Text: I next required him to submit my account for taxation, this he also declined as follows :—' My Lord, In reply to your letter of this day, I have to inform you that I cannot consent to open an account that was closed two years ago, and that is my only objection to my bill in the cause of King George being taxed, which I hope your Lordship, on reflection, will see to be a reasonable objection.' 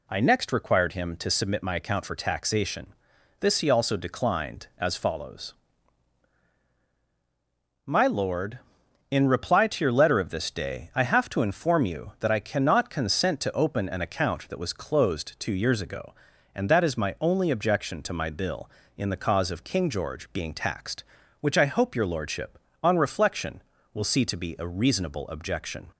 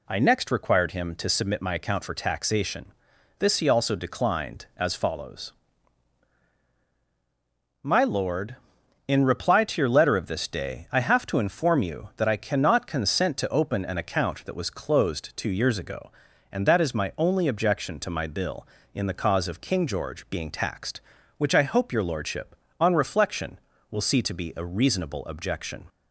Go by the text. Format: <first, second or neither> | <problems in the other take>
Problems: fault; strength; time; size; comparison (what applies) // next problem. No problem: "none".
neither | none